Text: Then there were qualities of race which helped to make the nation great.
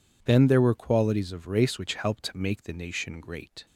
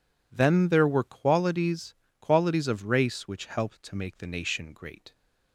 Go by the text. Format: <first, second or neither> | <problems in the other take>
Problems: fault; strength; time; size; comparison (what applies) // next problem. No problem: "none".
first | says "qualities" twice; at 2.1 s